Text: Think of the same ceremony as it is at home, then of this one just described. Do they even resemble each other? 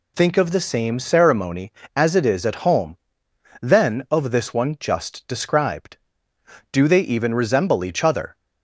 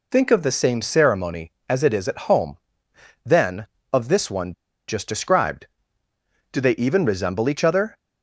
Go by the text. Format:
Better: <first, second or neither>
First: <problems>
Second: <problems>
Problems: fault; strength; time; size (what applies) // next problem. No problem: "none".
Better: first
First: none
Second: pauses between "one" and "just"; at 4.5 s; 0.36 s long